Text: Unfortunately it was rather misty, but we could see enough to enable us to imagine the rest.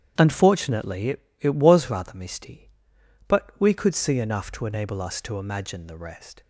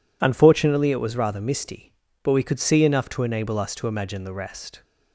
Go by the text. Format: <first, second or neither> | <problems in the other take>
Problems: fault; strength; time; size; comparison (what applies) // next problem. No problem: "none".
second | starts louder than the rest; strong; until 1.1 s; 9.5 dB // says "it" twice; at 1.3 s